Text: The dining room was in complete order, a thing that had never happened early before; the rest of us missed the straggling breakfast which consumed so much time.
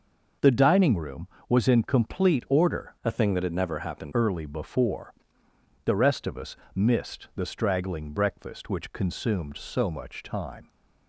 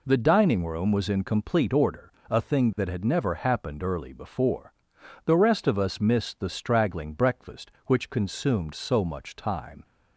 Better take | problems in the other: second | starts louder than the rest; noticeable; until 1.6 s; 6 dB // changes voice from "a" to "happened"; from 3.0 to 4.1 s; 1.1 s long // pauses between "us" and "missed"; slight; at 6.5 s; 0.20 s long

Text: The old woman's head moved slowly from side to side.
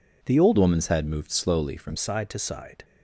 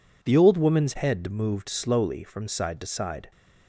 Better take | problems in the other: second | changes voice from "woman's" to "from"; from 0.5 to 1.9 s; 1.4 s long

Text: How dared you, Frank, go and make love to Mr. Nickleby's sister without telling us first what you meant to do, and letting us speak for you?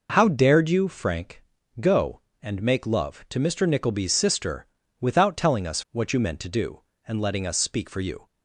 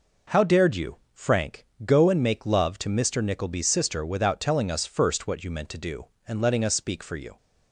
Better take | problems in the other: second | pauses between "sister" and "without"; slight; at 4.6 s; 0.32 s long // skips "first"; at 5.8 s

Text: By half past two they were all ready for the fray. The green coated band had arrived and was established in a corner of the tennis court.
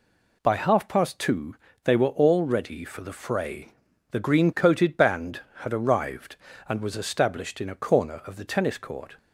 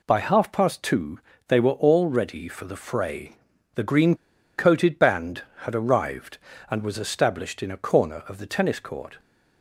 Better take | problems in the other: first | pauses between "two" and "they"; slight; at 1.2 s; 0.26 s long; slight in the first // pauses between "green" and "coated"; at 4.1 s; 0.41 s long

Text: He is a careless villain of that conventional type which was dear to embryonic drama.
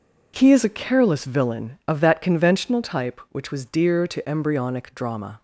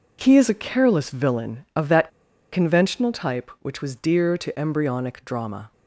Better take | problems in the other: first | pauses between "that" and "conventional"; at 2.0 s; 0.42 s long

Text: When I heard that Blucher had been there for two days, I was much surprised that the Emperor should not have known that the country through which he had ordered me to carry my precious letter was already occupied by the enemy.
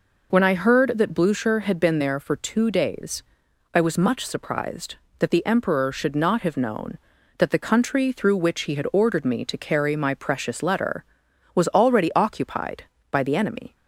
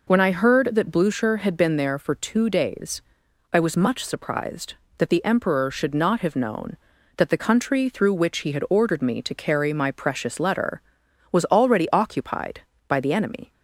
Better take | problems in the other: neither | none

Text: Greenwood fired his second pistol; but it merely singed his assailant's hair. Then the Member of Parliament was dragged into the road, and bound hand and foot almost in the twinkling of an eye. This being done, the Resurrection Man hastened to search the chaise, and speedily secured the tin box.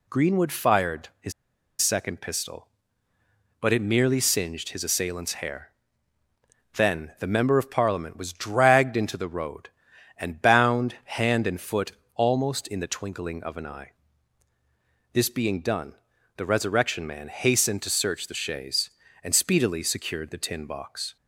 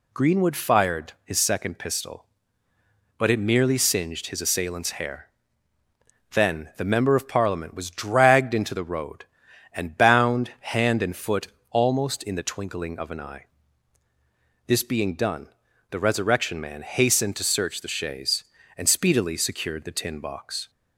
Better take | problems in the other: second | pauses between "his" and "second"; noticeable; at 1.3 s; 0.49 s long // pauses between "foot" and "almost"; slight; at 11.8 s; 0.24 s long; slight in the second

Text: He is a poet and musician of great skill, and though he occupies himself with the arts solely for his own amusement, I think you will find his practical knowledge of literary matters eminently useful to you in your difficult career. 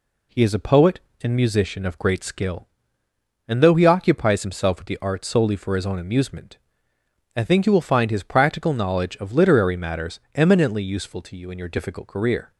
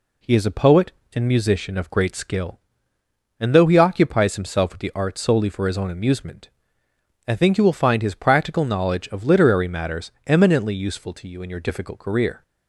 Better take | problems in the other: neither | pauses between "matters" and "eminently"; slight; the same in both

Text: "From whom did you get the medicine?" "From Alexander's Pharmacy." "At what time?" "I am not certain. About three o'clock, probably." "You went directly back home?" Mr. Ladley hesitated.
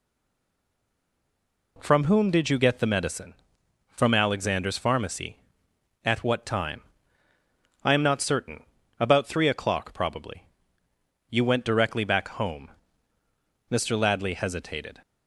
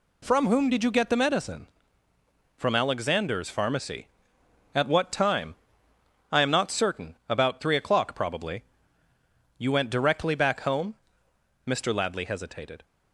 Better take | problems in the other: second | stays silent before the first word; noticeable; until 1.7 s; 1.7 s long

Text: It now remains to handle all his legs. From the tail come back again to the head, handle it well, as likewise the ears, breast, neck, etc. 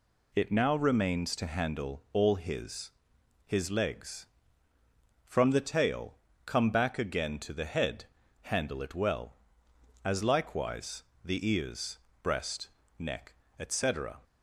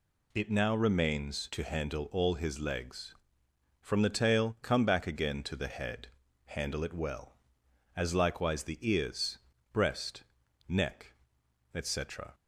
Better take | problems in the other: second | says "his" twice; at 3.4 s // pauses between "tail" and "come"; slight; at 6.1 s; 0.32 s long // pauses between "likewise" and "the"; slight; at 11.0 s; 0.20 s long

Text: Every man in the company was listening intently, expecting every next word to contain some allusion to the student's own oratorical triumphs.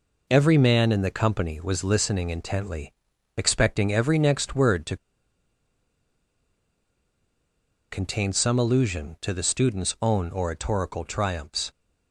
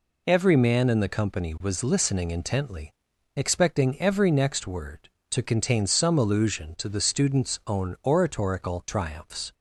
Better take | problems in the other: second | pauses between "to" and "contain"; strong; at 4.9 s; 2.9 s long

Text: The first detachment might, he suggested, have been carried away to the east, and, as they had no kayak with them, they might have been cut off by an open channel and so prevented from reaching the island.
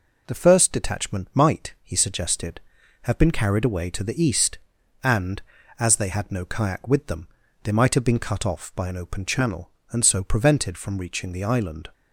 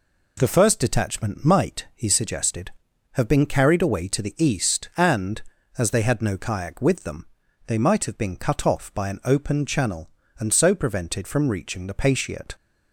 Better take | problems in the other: first | says "patiate" for "island"; at 11.9 s

